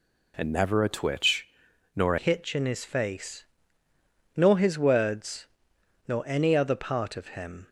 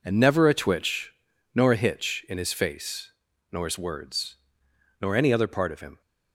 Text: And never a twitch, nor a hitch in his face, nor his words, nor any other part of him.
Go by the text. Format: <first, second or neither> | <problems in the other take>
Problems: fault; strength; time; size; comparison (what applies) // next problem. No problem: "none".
second | changes voice at "hitch"; from 2.1 s on; 5.5 s long